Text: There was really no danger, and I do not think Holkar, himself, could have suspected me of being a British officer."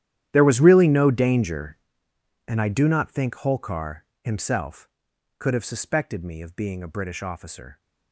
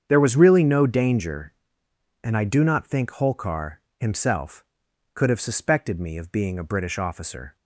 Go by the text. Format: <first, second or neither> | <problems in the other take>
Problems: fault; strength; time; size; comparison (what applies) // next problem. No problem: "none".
second | gets quieter; strong; throughout; 18.5 dB // starts louder than the rest; strong; until 1.3 s; 11.5 dB; strong in the second